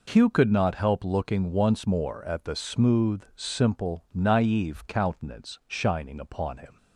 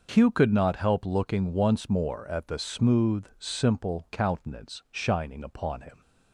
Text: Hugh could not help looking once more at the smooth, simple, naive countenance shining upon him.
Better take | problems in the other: first | starts louder than the rest; noticeable; until 1.1 s; 6 dB // skips "naive"; at 4.0 s

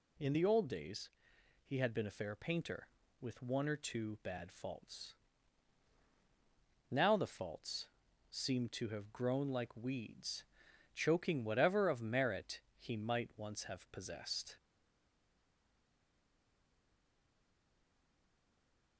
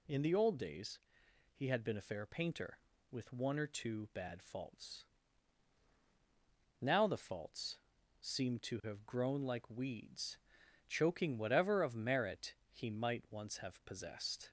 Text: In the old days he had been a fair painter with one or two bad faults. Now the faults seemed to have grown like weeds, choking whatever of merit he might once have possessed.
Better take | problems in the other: second | pauses between "days" and "he"; noticeable; at 1.0 s; 0.56 s long; noticeable in the second // pauses between "faults" and "seemed"; at 7.8 s; 0.42 s long; also in the second // pauses between "merit" and "he"; slight; at 12.5 s; 0.18 s long; slight in the second // stays silent after the last word; strong; from 14.5 s on; 4.4 s long

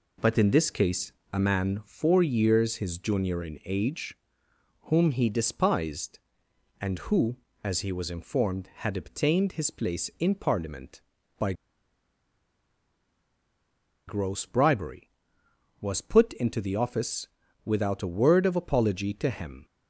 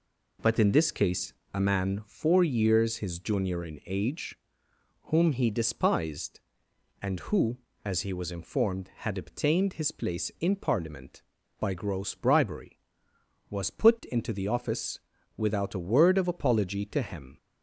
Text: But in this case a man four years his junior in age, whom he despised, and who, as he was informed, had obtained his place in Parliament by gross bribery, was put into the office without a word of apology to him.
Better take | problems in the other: second | pauses between "case" and "a"; slight; at 1.1 s; 0.20 s long; slight in the second // pauses between "by" and "gross"; strong; at 11.5 s; 2.5 s long // pauses between "office" and "without"; at 17.2 s; 0.38 s long; also in the second

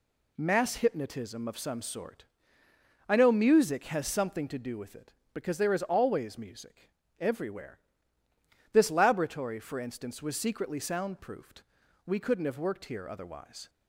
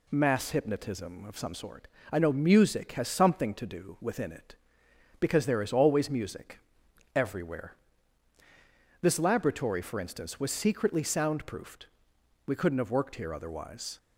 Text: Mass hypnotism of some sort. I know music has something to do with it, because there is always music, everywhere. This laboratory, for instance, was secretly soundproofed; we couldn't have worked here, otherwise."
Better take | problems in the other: first | says "within" for "with"; at 3.9 s

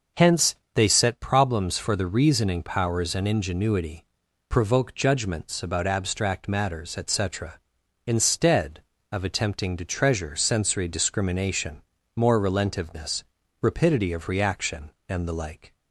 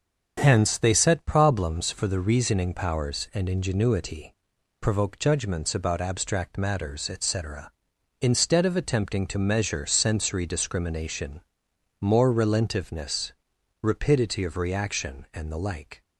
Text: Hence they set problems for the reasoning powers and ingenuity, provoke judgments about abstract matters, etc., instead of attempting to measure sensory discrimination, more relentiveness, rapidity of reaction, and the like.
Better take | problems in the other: second | starts louder than the rest; until 1.3 s; 6.5 dB; also in the second // pauses between "Hence" and "they"; slight; at 0.5 s; 0.22 s long // says "treasure" for "measure"; at 9.8 s

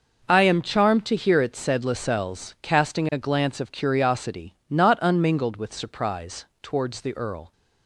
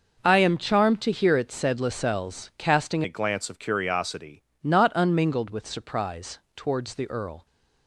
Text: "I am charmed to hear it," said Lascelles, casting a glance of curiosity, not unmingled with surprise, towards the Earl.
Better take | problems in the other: first | starts louder than the rest; noticeable; until 1.2 s; 6 dB // changes voice from "a" to "curiosity"; from 3.0 to 4.4 s; 1.4 s long

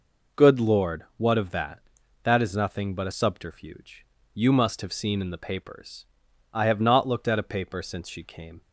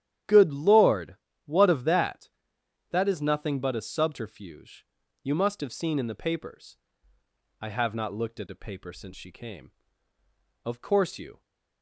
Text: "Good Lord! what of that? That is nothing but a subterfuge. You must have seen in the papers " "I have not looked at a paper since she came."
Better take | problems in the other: first | starts louder than the rest; strong; until 1.5 s; 12 dB // goes on to say "Of course you"; noticeable; from 10.6 s on; 0.76 s long

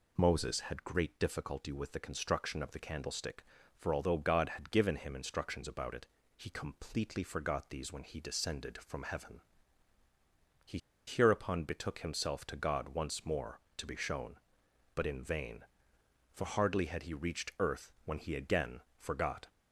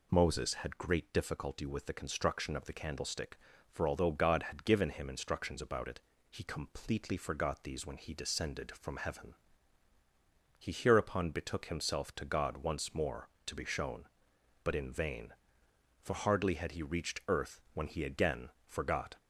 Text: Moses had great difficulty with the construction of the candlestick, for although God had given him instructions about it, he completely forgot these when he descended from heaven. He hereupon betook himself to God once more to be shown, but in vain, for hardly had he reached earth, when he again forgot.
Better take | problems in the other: second | pauses between "He" and "hereupon"; slight; at 10.7 s; 0.29 s long // pauses between "again" and "forgot"; slight; at 18.8 s; 0.18 s long; slight in the second

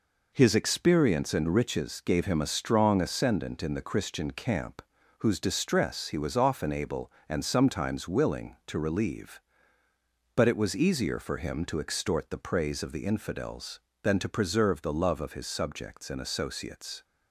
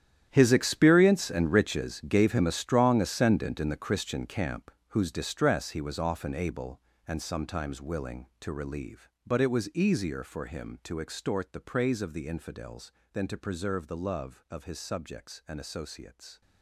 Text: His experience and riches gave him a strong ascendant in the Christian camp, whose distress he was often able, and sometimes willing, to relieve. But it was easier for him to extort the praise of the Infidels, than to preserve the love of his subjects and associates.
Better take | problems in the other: first | gets quieter; strong; throughout; 15.5 dB

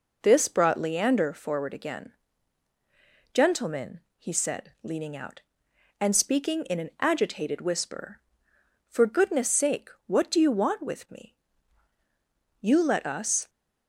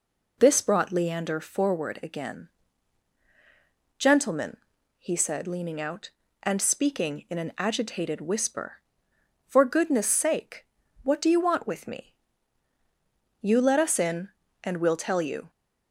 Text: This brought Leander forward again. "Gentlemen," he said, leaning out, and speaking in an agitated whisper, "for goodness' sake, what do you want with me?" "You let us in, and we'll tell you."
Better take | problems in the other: second | stops before "in and we'll tell you"; at 13.4 s

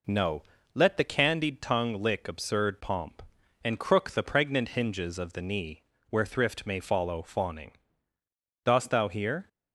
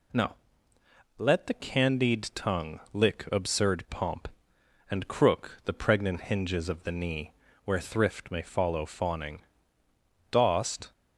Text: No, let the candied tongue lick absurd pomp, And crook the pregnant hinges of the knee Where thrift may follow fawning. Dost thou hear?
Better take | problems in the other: first | pauses between "knee" and "Where"; slight; at 7.3 s; 0.32 s long; slight in the first // stops before "thou hear"; at 10.9 s

